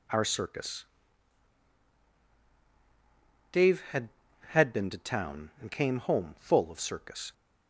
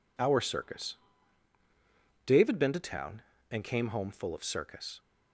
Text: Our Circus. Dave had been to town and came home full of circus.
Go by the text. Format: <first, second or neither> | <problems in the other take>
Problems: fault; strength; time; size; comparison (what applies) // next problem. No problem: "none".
second | says "had" twice; at 4.4 s